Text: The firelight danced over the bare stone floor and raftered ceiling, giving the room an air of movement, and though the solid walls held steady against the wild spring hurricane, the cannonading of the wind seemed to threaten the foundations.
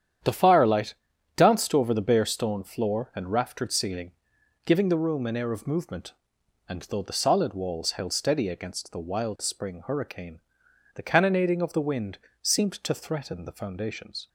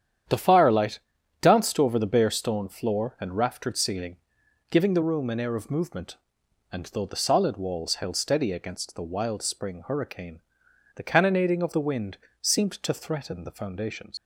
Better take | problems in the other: first | starts louder than the rest; strong; until 1.7 s; 9.5 dB; strong in the first // pauses between "firelight" and "danced"; at 0.9 s; 0.42 s long; also in the first // pauses between "wind" and "seemed"; slight; at 12.1 s; 0.24 s long; slight in the first // leaves "foundations" unfinished; at 14.1 s; 100 ms

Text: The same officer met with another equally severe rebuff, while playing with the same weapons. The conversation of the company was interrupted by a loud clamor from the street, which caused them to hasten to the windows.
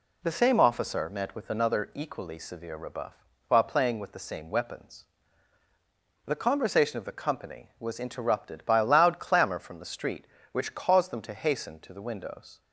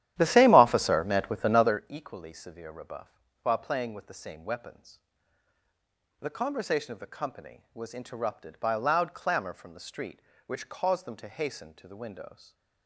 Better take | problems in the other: first | starts louder than the rest; strong; until 1.8 s; 12.5 dB

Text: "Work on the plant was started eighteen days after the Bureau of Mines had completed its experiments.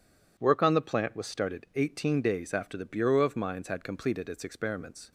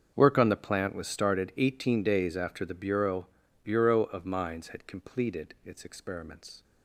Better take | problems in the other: first | starts louder than the rest; strong; until 1.1 s; 7 dB // says "Bureau" twice; at 3.6 s

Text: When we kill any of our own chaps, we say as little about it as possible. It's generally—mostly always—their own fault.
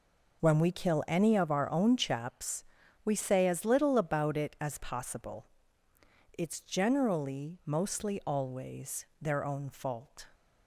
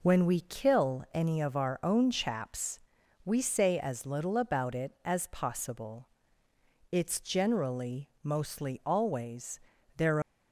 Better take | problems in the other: first | stops before "own fault"; at 10.2 s

